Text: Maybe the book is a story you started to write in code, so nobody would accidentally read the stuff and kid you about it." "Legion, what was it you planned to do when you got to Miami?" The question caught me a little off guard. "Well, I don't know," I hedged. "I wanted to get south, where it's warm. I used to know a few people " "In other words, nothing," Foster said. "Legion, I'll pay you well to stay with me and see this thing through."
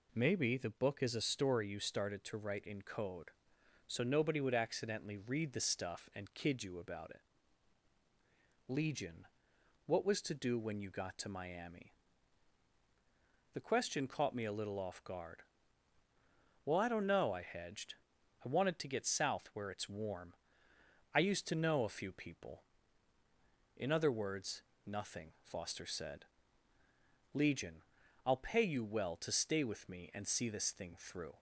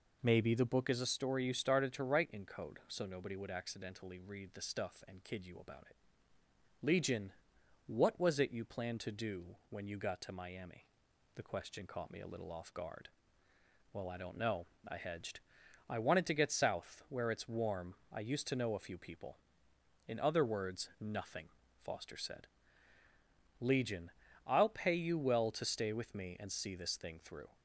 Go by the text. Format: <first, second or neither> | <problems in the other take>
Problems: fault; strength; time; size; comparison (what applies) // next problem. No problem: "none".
second | skips "it you planned"; at 10.2 s